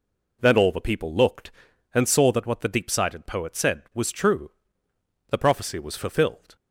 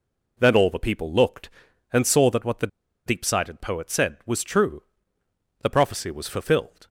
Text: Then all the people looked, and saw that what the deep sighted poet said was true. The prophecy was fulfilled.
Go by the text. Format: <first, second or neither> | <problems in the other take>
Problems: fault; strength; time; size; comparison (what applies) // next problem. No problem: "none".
first | pauses between "the" and "deep"; at 2.6 s; 0.39 s long